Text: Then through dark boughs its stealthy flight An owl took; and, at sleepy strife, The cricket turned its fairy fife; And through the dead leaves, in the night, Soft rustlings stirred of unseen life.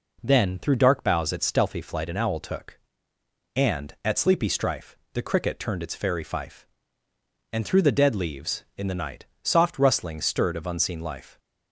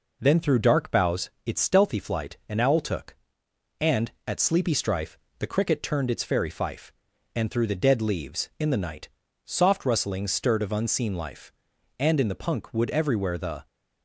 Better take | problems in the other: first | pauses between "boughs" and "its"; slight; at 1.2 s; 0.16 s long // goes on to say "And in the punk wood everywhere The"; from 11.9 s on; 1.6 s long

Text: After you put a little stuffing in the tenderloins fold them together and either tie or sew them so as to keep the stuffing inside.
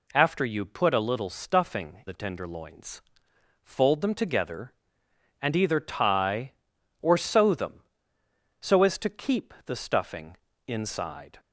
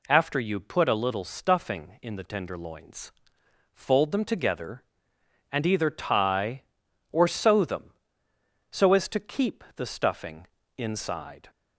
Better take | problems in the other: second | skips "in"; at 2.0 s // pauses between "tenderloins" and "fold"; noticeable; at 3.0 s; 0.62 s long; noticeable in the second // pauses between "stuffing" and "inside"; slight; at 10.3 s; 0.30 s long; slight in the second

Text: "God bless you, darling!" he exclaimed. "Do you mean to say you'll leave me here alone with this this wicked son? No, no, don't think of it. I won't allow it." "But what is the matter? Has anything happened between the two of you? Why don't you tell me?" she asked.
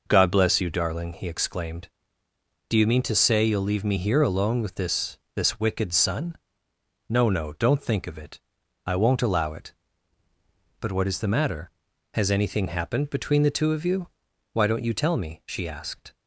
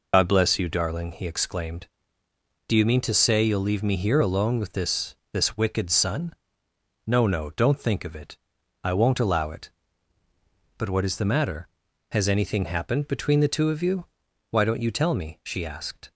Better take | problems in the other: first | loses the start of "God"; at 0.1 s; 105 ms // pauses between "this" and "this"; slight; at 5.1 s; 0.16 s long; slight in the first

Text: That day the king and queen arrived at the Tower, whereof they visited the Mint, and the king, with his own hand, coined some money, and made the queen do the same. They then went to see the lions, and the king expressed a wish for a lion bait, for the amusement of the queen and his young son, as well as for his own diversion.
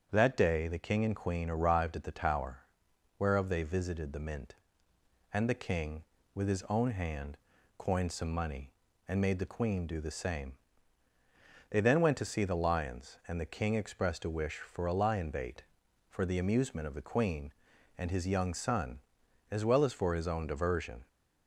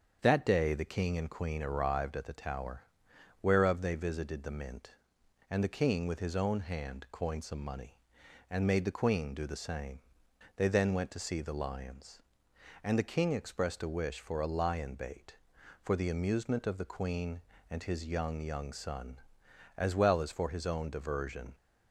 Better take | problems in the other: first | starts louder than the rest; strong; until 1.2 s; 7 dB; also in the first // says "young" twice; at 18.4 s

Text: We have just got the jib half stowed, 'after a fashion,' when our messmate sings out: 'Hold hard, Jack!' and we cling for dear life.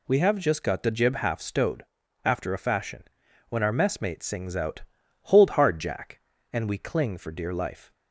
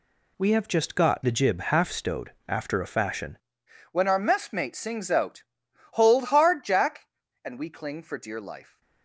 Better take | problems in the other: first | changes voice at "when"; from 3.9 s on; 4.9 s long

